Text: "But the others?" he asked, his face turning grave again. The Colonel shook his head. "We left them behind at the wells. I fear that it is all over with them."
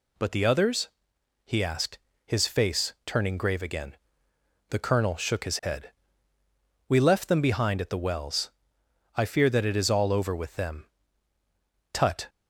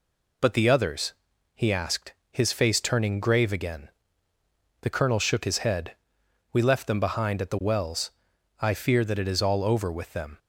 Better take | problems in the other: second | goes on to say "Tut"; slight; from 11.9 s on; 0.36 s long

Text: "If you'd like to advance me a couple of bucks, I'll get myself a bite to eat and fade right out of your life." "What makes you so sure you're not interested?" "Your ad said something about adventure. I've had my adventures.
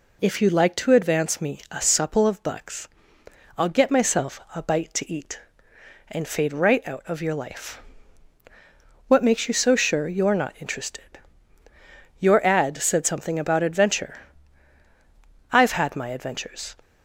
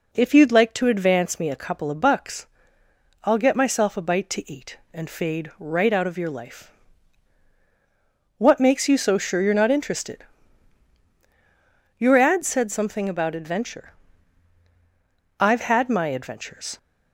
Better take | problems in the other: second | says "supple" for "couple"; at 1.8 s // pauses between "myself" and "a"; slight; at 4.3 s; 0.16 s long

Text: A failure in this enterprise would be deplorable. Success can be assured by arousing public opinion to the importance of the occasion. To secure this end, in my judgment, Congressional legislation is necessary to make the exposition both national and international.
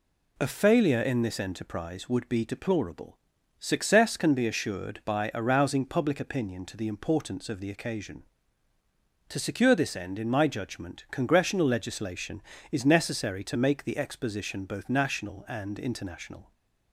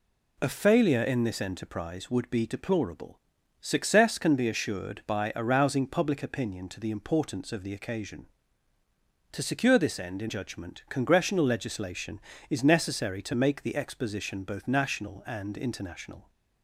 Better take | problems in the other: first | skips "my"; at 10.2 s

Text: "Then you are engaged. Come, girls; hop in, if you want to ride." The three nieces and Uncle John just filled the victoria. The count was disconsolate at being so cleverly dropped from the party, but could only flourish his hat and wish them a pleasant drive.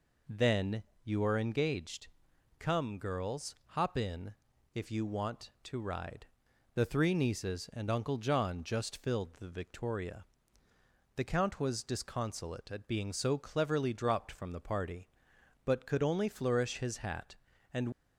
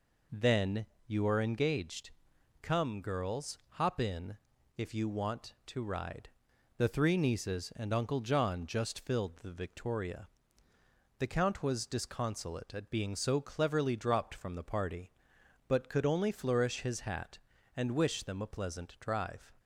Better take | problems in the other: second | pauses between "Then" and "you"; slight; at 0.8 s; 0.22 s long; slight in the second // stops before "wish them a pleasant drive"; at 17.9 s

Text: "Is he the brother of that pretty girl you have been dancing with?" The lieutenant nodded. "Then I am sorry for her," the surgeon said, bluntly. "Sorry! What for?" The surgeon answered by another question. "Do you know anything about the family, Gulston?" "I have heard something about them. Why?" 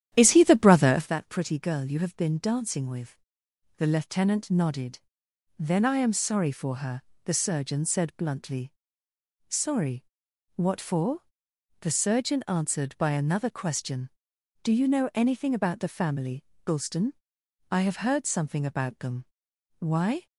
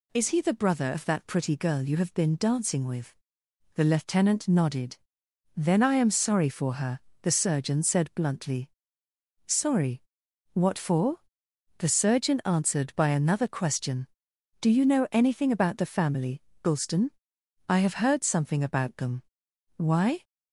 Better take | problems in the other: second | starts louder than the rest; strong; until 1.1 s; 11 dB

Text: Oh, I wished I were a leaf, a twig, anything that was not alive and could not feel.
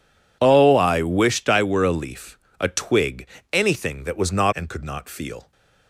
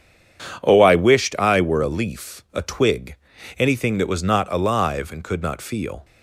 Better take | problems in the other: second | skips "alive"; at 4.5 s

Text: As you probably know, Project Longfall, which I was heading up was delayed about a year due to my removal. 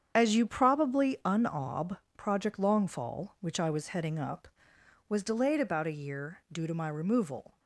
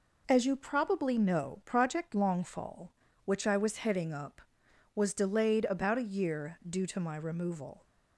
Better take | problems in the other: second | starts louder than the rest; strong; until 1.1 s; 8 dB // says "unob" for "know"; at 1.2 s

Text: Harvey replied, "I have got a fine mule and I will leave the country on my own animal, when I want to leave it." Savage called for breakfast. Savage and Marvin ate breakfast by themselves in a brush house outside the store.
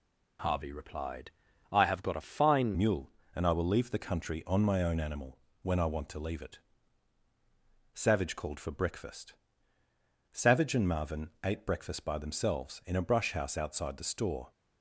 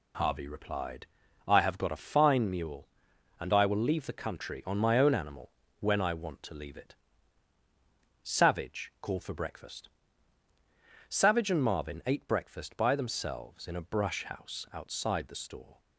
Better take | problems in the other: second | changes voice at "mule"; from 2.7 s on; 11.8 s long

